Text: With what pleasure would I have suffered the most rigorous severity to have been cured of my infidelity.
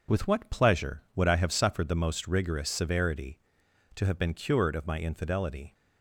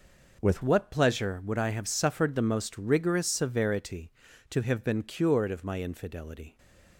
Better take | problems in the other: first | changes voice at "what"; from 0.6 s on; 5.9 s long // stays silent after the last word; slight; from 6.4 s on; 0.5 s long

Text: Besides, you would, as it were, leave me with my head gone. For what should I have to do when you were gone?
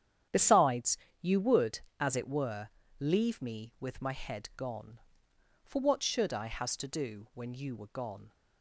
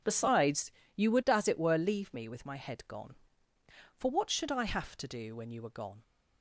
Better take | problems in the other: second | starts louder than the rest; strong; until 1.5 s; 9.5 dB // says "has" for "have"; at 6.4 s

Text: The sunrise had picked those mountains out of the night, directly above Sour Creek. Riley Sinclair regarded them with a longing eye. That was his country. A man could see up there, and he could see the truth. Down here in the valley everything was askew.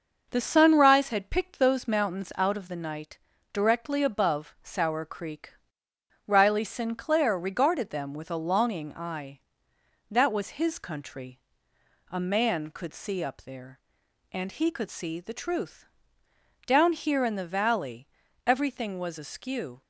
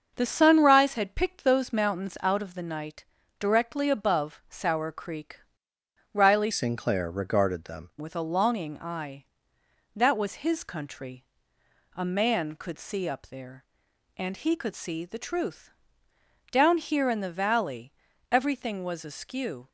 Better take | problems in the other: first | starts louder than the rest; until 1.1 s; 6.5 dB // changes voice from "Sinclair" to "them"; from 6.5 to 7.8 s; 1.3 s long // pauses between "valley" and "everything"; slight; at 17.9 s; 0.36 s long; slight in the first

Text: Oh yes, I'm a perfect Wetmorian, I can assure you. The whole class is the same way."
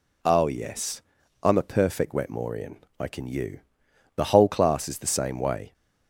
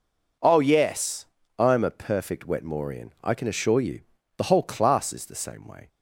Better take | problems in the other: second | skips "assure"; at 3.2 s

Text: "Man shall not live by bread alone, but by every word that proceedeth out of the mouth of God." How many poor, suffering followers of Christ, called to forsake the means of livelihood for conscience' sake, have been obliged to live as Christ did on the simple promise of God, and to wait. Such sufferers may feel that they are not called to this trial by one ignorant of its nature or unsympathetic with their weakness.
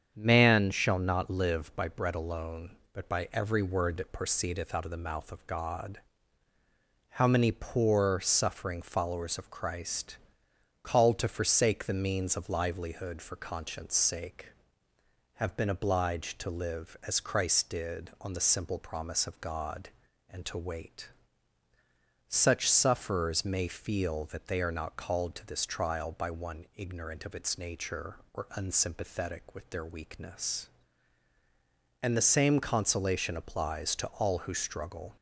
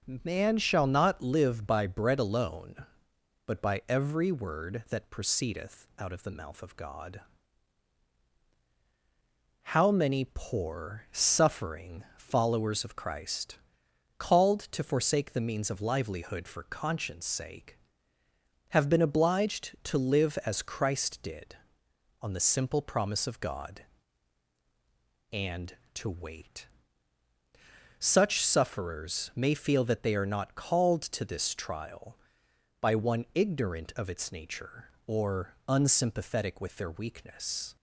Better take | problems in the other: second | starts louder than the rest; strong; until 1.1 s; 7.5 dB // goes on to say "And the same consolation applies to all who struggle"; strong; from 32.0 s on; 3.1 s long

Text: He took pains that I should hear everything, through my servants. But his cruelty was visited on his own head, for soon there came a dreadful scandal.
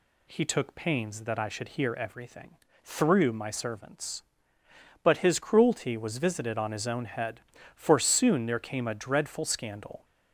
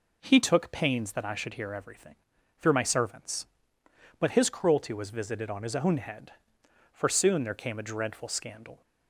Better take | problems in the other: neither | none

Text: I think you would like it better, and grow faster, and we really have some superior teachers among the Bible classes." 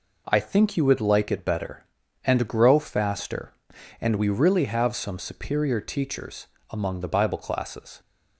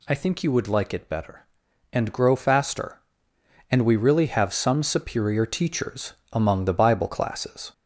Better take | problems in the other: first | gets louder; slight; throughout; 2.5 dB // pauses between "teachers" and "among"; slight; at 6.1 s; 0.18 s long; slight in the first

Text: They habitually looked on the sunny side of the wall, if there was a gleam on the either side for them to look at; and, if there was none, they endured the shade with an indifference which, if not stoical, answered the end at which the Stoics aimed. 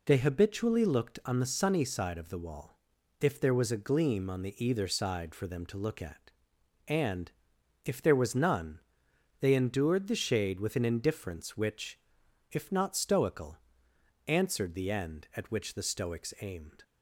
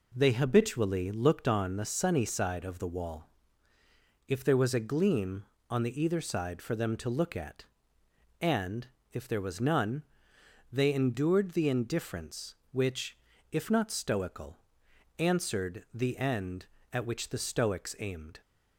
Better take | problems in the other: first | skips "shade with an"; at 11.6 s

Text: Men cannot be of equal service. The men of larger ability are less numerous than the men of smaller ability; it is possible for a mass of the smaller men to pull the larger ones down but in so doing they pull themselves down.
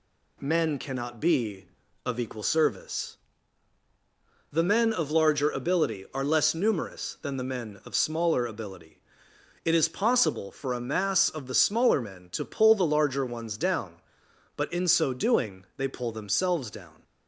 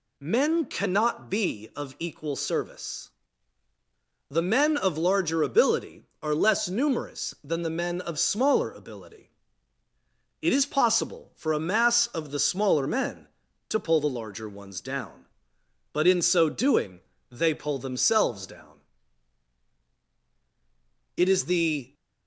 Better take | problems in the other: first | pauses between "doing" and "they"; slight; at 16.9 s; 0.30 s long // goes on to say "It is the"; noticeable; from 21.1 s on; 0.78 s long

